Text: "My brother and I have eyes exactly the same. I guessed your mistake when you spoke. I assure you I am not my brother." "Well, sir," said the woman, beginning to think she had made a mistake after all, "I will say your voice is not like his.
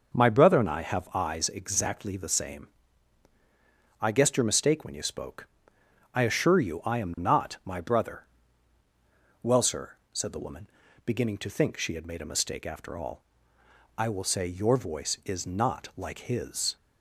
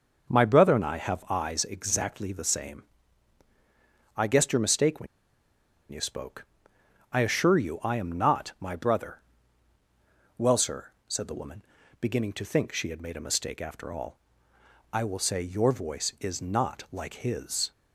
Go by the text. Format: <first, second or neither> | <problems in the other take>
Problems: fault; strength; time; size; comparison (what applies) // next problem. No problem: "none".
first | pauses between "when" and "you"; noticeable; at 5.0 s; 0.84 s long